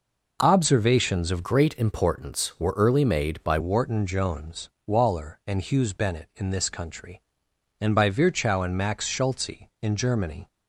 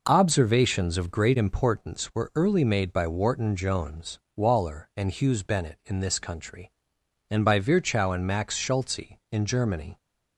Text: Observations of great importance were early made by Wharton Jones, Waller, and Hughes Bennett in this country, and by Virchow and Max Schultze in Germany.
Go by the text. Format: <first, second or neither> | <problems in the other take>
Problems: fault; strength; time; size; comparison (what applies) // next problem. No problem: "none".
second | changes voice from "great" to "by"; from 1.4 to 3.5 s; 2.1 s long